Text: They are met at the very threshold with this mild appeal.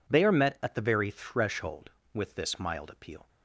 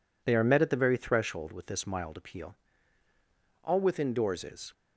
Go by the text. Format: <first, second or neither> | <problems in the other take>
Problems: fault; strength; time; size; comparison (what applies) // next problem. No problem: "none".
first | goes on to say "All within doors is"; noticeable; from 3.6 s on; 1.1 s long